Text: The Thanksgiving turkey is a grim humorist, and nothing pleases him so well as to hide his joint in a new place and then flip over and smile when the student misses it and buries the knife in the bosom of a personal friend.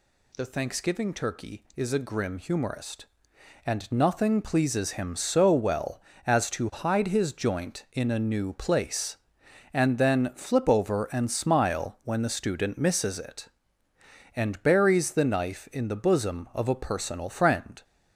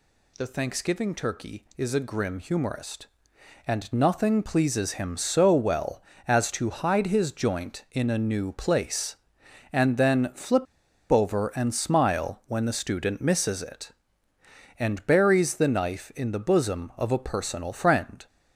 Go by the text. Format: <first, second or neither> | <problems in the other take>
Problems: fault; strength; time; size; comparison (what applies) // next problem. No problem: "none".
first | pauses between "flip" and "over"; noticeable; at 10.6 s; 0.47 s long